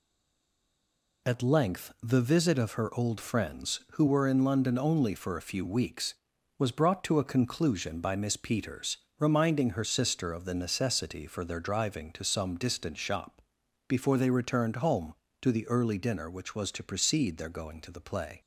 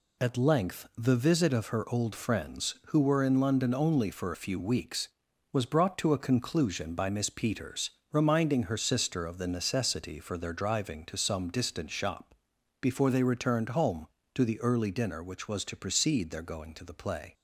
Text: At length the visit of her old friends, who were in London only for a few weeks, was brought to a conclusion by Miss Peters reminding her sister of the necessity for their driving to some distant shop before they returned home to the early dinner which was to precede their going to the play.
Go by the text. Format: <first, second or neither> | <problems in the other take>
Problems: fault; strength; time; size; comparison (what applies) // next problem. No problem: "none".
second | stays silent before the first word; noticeable; until 1.2 s; 1.2 s long // pauses between "Peters" and "reminding"; slight; at 8.9 s; 0.22 s long; slight in the second // pauses between "shop" and "before"; noticeable; at 13.4 s; 0.48 s long; noticeable in the second